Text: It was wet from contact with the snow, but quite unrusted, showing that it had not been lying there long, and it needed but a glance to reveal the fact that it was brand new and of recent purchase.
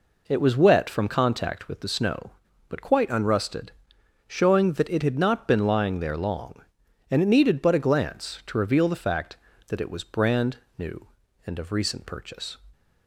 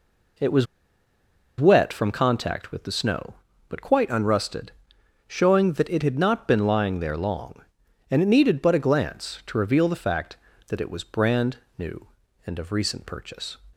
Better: first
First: pauses between "brand" and "new"; slight; at 10.5 s; 0.18 s long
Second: pauses between "was" and "wet"; noticeable; at 0.6 s; 0.94 s long // pauses between "brand" and "new"; slight; at 11.5 s; 0.18 s long

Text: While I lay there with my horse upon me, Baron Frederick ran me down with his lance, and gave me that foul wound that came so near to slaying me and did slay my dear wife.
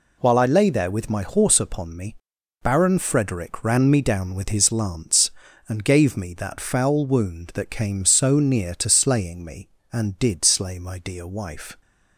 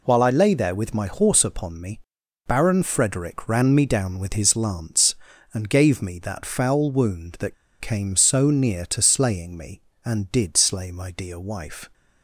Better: first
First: none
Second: pauses between "that" and "came"; slight; at 7.5 s; 0.25 s long

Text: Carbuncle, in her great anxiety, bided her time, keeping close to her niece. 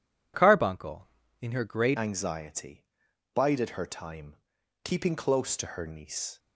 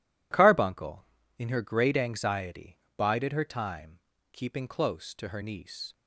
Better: second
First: changes voice at "anxiety"; from 1.9 s on; 4.4 s long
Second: none

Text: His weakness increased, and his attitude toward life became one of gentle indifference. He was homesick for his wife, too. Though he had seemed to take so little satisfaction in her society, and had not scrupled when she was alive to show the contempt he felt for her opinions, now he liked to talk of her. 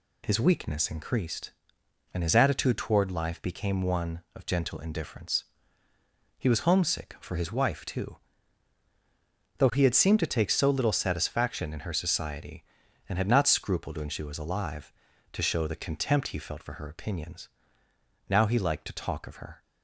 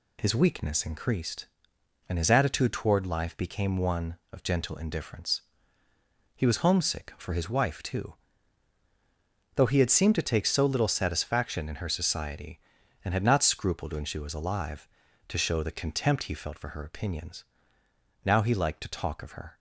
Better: neither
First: none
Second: none

